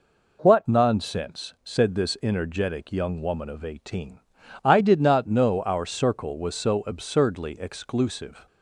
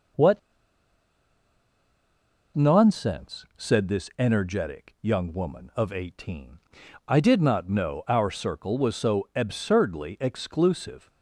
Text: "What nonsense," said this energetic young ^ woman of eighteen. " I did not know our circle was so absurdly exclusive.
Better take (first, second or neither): first